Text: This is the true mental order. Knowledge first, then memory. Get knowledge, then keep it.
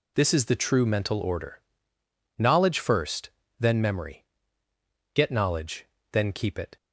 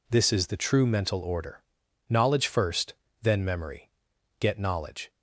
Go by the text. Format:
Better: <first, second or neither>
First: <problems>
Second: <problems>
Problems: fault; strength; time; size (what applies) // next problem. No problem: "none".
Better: first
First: none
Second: stops before "then keep it"; at 5.0 s